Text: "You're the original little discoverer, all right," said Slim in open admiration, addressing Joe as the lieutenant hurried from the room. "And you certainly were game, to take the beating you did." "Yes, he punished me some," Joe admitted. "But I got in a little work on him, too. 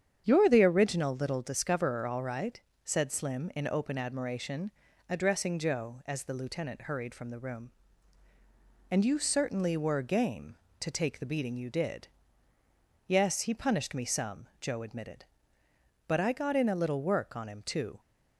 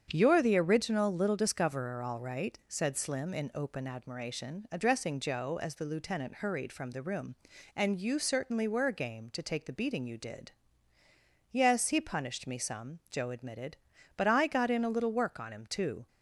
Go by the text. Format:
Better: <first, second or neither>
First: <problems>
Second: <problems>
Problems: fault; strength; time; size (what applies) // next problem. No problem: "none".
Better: neither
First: starts louder than the rest; strong; until 1.2 s; 8.5 dB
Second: starts louder than the rest; strong; until 1.1 s; 8 dB